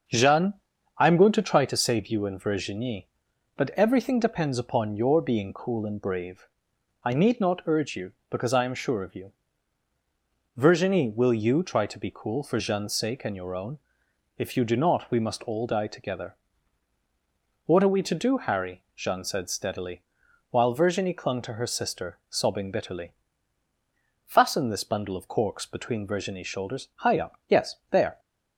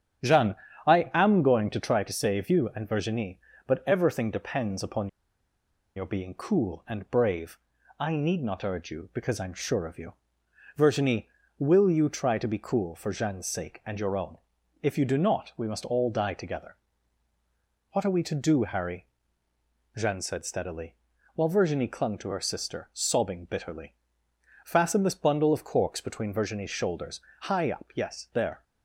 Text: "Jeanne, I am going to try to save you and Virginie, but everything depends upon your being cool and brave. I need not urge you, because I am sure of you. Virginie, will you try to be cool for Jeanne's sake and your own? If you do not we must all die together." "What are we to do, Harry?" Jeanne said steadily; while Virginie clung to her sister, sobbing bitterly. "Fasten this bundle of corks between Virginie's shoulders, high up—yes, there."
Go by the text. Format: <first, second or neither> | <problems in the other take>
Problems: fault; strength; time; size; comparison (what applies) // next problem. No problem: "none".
first | starts louder than the rest; strong; until 1.5 s; 9.5 dB; also in the first // pauses between "upon" and "your"; noticeable; at 5.0 s; 0.87 s long